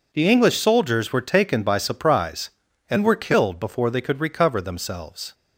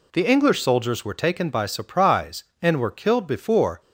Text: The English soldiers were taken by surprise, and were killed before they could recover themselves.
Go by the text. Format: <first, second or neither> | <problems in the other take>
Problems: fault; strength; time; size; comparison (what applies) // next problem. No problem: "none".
first | stops before "they could recover themselves"; at 3.8 s